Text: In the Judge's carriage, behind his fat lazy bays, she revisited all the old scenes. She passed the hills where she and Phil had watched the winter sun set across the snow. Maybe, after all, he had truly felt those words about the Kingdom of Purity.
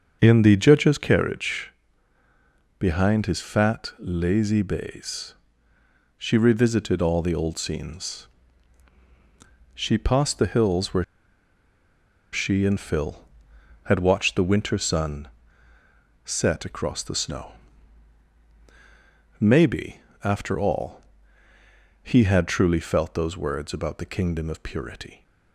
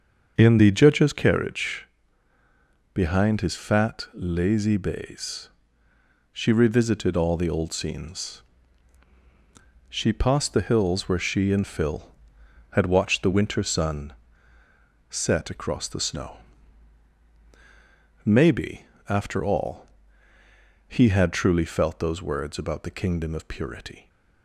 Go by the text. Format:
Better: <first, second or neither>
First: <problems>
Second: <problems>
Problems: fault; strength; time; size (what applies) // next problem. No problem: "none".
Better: second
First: starts louder than the rest; until 1.2 s; 7 dB // pauses between "where" and "she"; strong; at 11.0 s; 1.2 s long // pauses between "sun" and "set"; noticeable; at 15.2 s; 0.96 s long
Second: starts louder than the rest; until 1.3 s; 7 dB // pauses between "sun" and "set"; noticeable; at 14.1 s; 0.96 s long